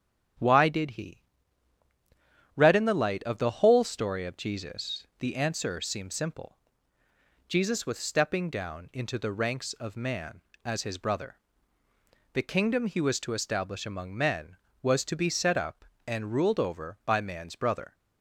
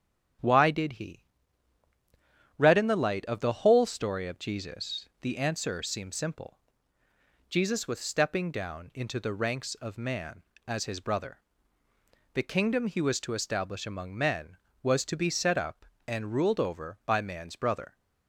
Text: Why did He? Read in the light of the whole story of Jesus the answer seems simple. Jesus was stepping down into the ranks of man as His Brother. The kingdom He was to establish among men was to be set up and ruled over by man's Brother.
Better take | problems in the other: neither | starts louder than the rest; strong; the same in both

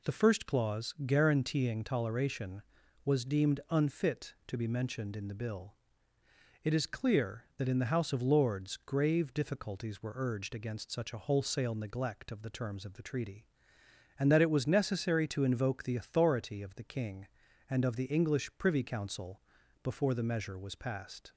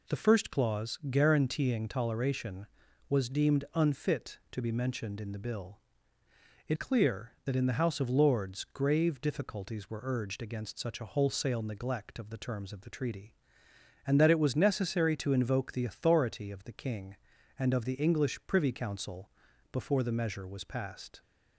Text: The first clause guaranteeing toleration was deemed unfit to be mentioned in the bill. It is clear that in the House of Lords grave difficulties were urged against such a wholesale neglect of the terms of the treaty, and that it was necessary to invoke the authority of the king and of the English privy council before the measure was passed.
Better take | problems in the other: first | skips "is"; at 6.7 s // pauses between "council" and "before"; at 19.3 s; 0.40 s long; also in the first

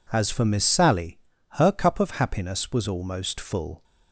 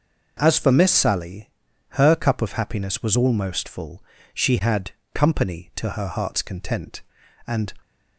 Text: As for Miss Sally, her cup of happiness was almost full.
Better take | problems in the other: first | starts louder than the rest; noticeable; until 1.4 s; 6 dB // goes on to say "She had company to her heart's content and"; strong; from 4.3 s on; 3.4 s long

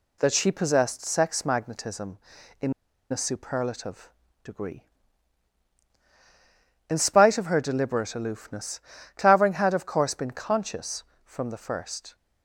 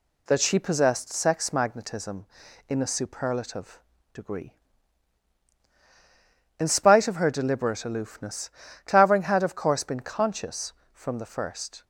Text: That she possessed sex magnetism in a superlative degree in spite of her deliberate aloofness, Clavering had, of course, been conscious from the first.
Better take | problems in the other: second | pauses between "in" and "a"; at 2.7 s; 0.38 s long // pauses between "superlative" and "degree"; slight; at 4.0 s; 0.34 s long; slight in the second

